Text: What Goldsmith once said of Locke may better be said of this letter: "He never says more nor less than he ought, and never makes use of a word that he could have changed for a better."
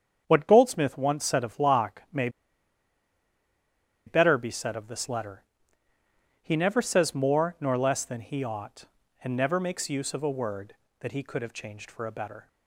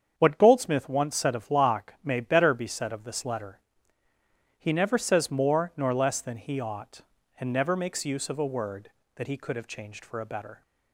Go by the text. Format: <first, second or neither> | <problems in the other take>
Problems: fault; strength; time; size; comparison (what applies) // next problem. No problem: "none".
second | starts louder than the rest; strong; until 1.2 s; 7.5 dB; strong in the second // pauses between "may" and "better"; strong; at 2.2 s; 1.7 s long